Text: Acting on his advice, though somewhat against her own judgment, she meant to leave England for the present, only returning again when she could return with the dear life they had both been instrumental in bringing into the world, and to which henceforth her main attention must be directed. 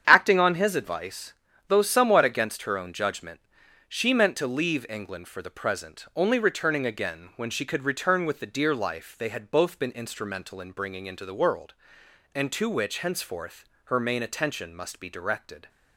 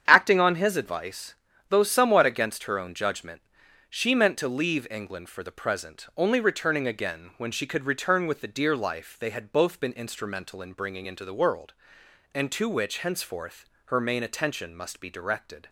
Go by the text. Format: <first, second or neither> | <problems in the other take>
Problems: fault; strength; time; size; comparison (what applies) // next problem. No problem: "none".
neither | starts louder than the rest; strong; the same in both // pauses between "henceforth" and "her"; slight; the same in both